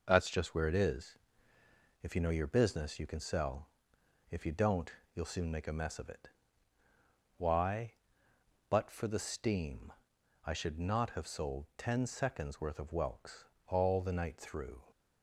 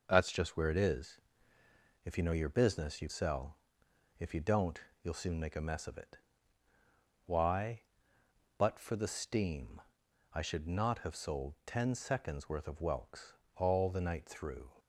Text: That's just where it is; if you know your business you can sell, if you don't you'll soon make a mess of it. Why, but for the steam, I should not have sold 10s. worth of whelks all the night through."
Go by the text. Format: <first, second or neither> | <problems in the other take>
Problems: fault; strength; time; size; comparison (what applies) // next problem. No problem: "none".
first | skips "can"; at 3.0 s // pauses between "don't" and "you'll"; slight; at 4.7 s; 0.22 s long; slight in the first // pauses between "whelks" and "all"; slight; at 13.3 s; 0.22 s long; slight in the first